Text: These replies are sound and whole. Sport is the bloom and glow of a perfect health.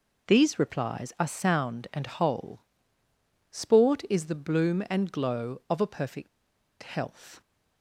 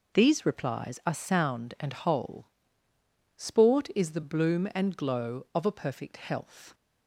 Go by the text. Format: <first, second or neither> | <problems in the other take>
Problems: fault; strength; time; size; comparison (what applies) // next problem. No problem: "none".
second | pauses between "perfect" and "health"; noticeable; at 6.2 s; 0.53 s long